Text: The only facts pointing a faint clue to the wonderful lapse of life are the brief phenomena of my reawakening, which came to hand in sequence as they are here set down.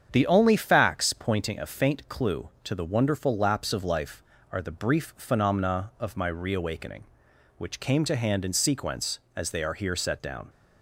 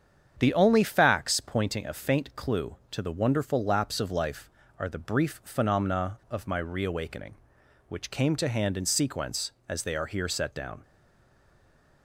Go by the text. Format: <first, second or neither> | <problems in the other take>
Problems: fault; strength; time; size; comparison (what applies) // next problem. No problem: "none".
first | starts louder than the rest; strong; until 1.4 s; 8 dB; strong in the first // stays silent after the last word; noticeable; from 10.8 s on; 1.2 s long